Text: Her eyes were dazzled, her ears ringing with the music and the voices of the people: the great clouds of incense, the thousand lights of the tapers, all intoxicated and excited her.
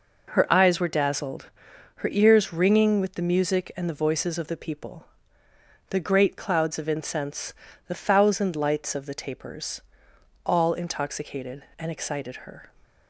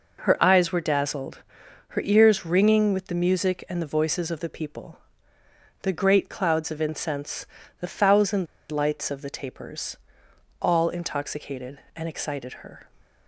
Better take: first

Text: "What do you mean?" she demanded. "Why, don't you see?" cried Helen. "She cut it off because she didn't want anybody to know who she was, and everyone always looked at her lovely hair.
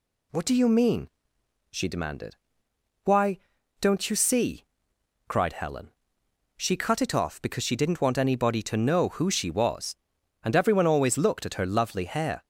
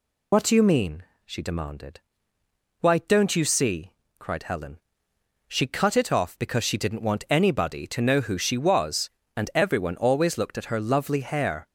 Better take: first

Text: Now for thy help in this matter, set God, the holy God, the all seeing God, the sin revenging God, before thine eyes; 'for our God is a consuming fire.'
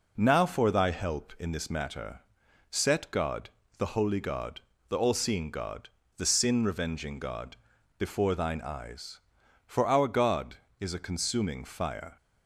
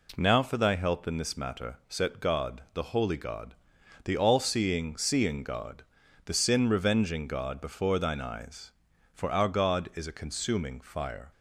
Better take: first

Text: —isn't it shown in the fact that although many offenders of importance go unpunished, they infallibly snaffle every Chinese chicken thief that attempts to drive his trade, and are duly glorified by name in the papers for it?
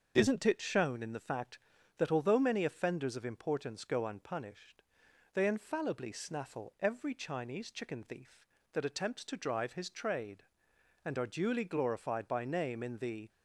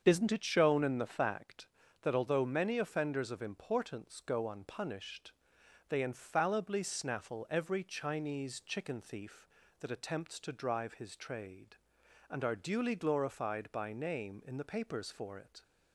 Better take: second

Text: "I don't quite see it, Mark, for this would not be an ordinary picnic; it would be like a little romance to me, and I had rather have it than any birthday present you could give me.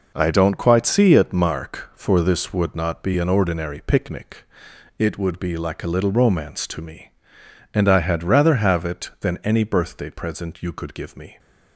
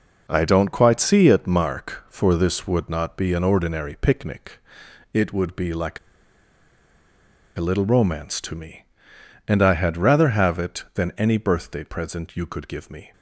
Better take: first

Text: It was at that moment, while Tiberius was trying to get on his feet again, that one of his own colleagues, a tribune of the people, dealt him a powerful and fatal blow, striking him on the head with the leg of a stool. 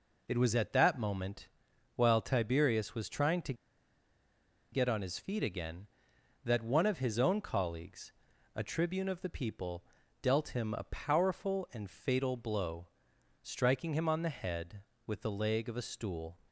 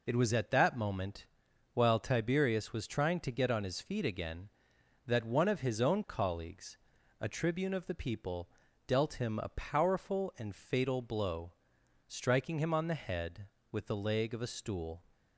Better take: second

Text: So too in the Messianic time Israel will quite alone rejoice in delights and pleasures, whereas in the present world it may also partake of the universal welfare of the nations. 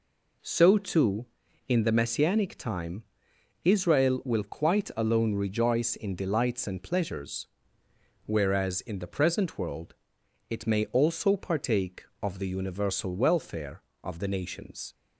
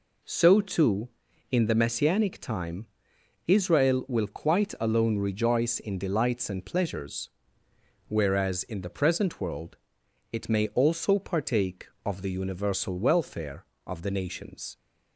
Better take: neither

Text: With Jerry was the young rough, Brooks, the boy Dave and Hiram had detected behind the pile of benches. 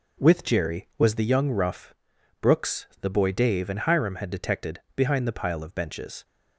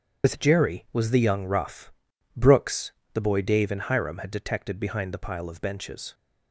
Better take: first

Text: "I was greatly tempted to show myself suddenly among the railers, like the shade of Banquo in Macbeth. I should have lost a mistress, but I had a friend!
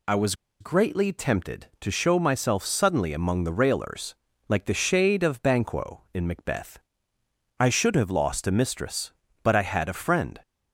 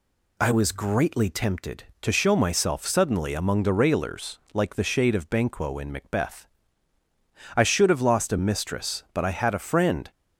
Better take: second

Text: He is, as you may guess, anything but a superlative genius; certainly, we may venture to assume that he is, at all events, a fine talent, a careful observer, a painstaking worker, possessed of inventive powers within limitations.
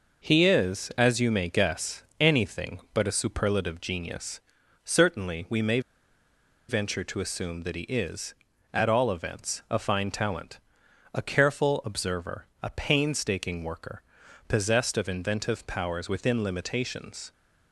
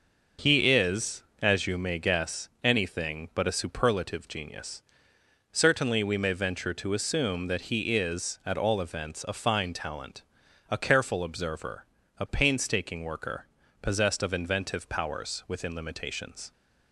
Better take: second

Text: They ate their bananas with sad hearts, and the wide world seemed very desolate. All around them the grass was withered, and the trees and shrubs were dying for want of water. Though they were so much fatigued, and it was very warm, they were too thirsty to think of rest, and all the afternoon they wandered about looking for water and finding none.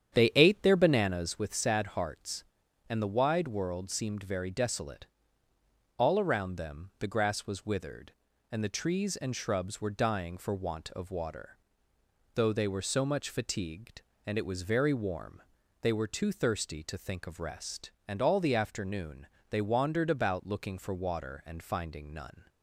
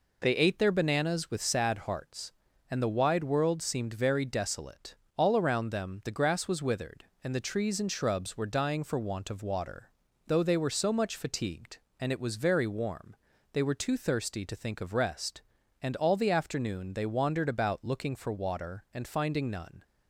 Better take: second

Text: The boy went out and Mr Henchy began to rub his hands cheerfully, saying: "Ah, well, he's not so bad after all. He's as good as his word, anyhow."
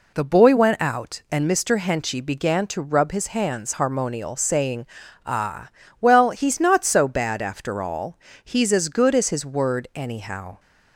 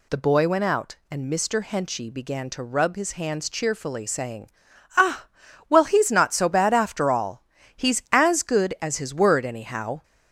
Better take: second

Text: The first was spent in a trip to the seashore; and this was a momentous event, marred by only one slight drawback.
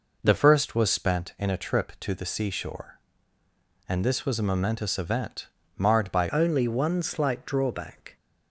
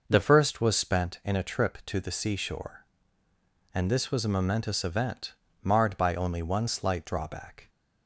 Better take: second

